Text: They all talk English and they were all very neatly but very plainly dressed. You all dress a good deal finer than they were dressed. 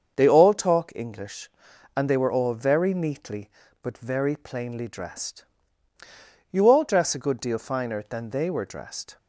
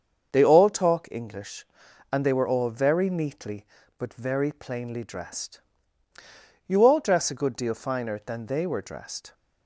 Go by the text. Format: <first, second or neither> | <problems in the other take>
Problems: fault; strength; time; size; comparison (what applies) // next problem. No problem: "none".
neither | starts louder than the rest; the same in both